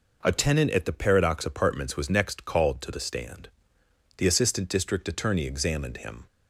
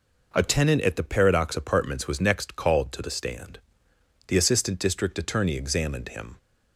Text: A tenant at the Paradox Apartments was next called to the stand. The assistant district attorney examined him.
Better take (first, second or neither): neither